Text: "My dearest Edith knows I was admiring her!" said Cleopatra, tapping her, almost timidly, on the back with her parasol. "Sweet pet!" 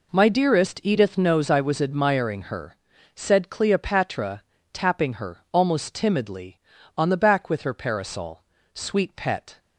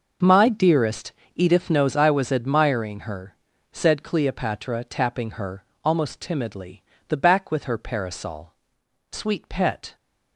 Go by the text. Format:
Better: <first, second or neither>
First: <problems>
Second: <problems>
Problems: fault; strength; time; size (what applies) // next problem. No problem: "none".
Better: first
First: none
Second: pauses between "dearest" and "Edith"; slight; at 1.1 s; 0.20 s long // skips "on"; at 6.9 s